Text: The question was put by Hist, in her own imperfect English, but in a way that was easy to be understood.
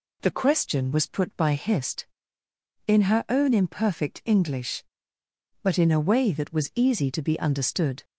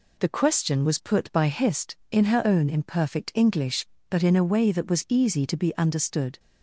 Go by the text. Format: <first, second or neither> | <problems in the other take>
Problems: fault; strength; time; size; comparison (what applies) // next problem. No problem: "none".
neither | none